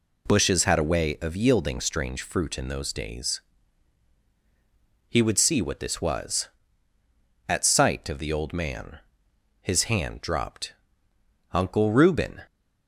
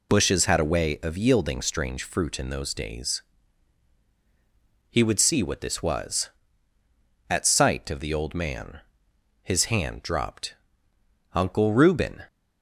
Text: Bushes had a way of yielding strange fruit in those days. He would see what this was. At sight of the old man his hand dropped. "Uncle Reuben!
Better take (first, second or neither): first